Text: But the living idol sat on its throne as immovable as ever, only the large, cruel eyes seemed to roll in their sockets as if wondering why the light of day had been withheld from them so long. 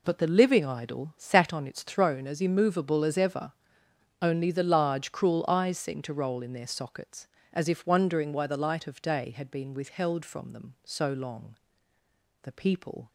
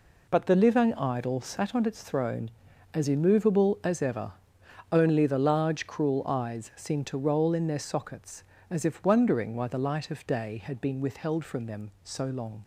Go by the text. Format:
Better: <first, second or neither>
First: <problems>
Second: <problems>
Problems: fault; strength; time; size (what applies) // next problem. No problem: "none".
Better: second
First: goes on to say "The people"; noticeable; from 12.4 s on; 0.66 s long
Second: none